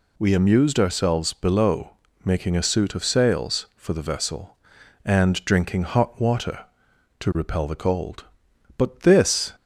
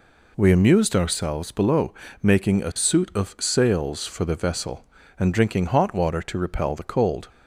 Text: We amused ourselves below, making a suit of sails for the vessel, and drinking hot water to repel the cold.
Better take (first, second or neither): second